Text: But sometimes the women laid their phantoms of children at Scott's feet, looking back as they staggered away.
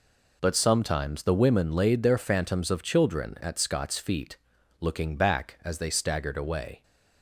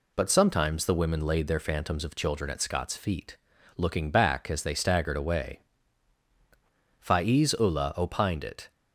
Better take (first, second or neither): first